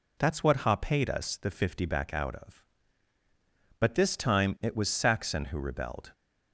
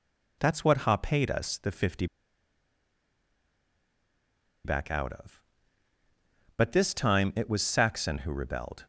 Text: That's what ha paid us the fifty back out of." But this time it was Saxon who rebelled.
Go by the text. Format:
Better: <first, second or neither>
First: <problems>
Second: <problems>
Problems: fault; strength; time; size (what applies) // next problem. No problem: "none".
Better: first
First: none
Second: pauses between "fifty" and "back"; strong; at 2.0 s; 2.5 s long